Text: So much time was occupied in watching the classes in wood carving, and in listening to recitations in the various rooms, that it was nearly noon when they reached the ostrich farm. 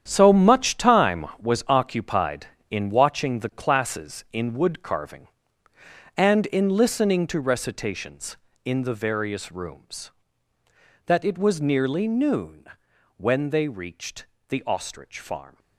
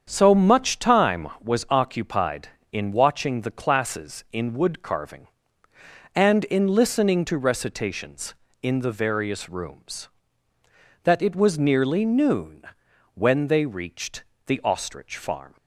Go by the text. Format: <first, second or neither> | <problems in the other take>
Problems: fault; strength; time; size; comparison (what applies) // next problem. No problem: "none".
second | gets quieter; strong; throughout; 11 dB // starts louder than the rest; strong; until 1.0 s; 9 dB; strong in the second // pauses between "noon" and "when"; noticeable; at 12.6 s; 0.52 s long; noticeable in the second // pauses between "reached" and "the"; slight; at 14.2 s; 0.24 s long; slight in the second